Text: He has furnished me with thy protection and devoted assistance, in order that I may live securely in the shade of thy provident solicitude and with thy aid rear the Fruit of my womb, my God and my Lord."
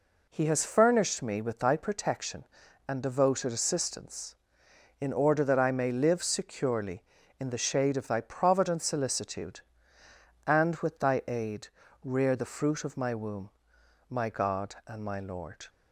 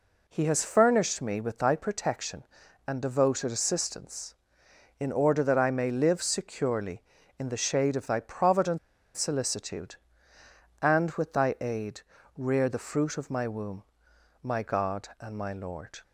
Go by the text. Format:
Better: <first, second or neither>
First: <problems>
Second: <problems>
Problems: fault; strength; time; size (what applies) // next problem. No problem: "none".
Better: first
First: pauses between "aid" and "rear"; slight; at 11.6 s; 0.36 s long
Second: pauses between "provident" and "solicitude"; at 8.7 s; 0.38 s long // pauses between "aid" and "rear"; slight; at 12.0 s; 0.36 s long